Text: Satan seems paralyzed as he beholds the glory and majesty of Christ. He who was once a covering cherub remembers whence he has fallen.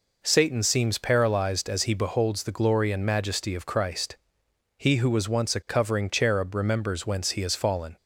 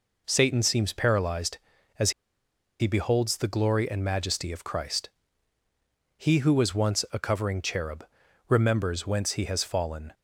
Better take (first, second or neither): first